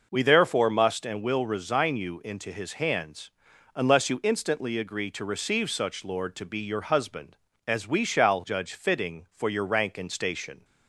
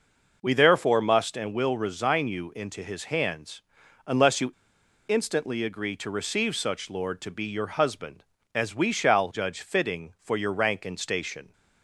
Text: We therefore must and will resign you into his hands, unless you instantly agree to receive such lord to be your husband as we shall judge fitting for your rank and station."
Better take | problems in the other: first | pauses between "you" and "instantly"; noticeable; at 4.5 s; 0.56 s long

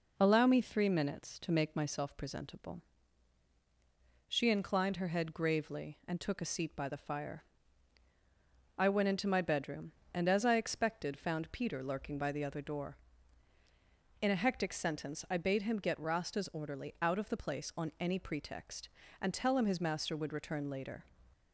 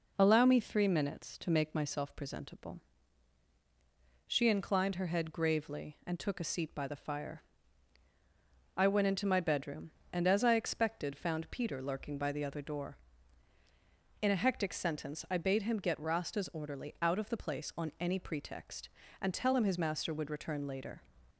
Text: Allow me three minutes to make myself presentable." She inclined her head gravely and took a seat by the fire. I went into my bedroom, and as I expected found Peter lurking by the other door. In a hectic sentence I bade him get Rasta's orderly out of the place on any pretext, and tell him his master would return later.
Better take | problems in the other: neither | none

